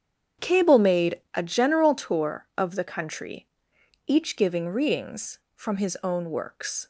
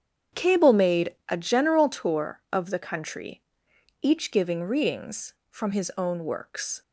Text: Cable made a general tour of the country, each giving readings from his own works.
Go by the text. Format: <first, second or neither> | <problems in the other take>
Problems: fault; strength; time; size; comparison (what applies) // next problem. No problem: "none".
neither | starts louder than the rest; strong; the same in both